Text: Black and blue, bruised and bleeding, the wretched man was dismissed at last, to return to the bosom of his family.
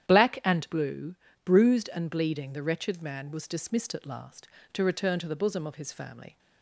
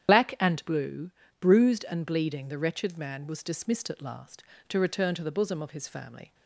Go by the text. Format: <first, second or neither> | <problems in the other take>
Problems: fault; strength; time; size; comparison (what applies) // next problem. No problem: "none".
first | loses the start of "Black"; at 0.0 s; 50 ms // starts louder than the rest; strong; until 1.4 s; 9.5 dB; strong in the first